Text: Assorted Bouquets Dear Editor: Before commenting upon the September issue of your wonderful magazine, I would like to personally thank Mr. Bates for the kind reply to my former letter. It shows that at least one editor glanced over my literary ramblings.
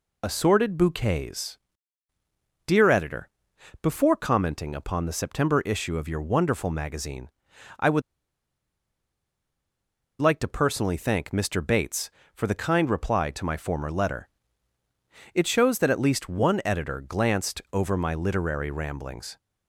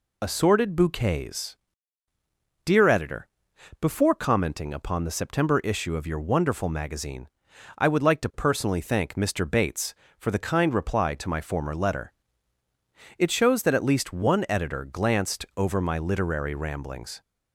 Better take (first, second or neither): second